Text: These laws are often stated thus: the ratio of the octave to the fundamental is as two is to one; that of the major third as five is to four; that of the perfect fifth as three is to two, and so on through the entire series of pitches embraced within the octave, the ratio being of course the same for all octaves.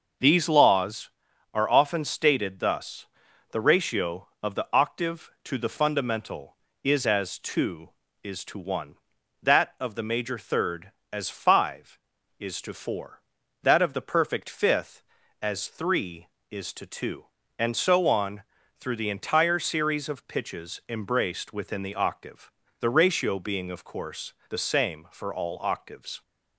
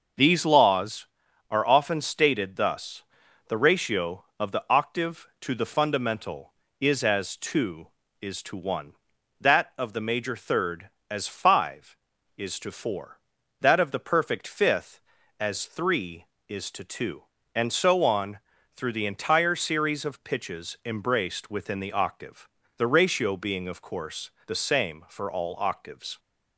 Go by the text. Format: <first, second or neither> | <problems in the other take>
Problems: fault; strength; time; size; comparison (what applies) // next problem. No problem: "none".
neither | starts louder than the rest; noticeable; the same in both // pauses between "on" and "through"; slight; the same in both // pauses between "course" and "the"; slight; the same in both